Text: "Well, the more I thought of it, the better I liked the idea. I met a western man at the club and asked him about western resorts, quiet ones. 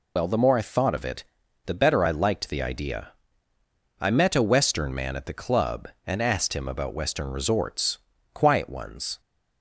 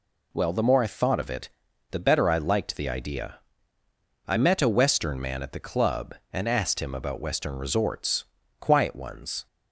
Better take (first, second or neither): second